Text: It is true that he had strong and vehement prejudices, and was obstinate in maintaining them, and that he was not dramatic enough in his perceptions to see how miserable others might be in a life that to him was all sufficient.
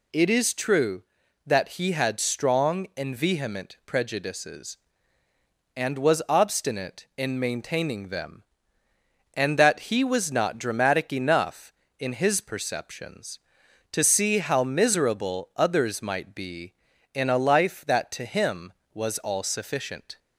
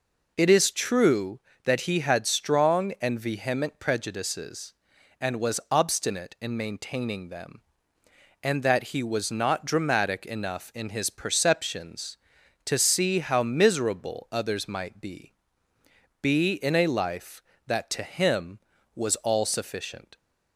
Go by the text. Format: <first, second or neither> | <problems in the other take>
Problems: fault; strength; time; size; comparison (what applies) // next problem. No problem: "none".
first | says "be" twice; at 16.2 s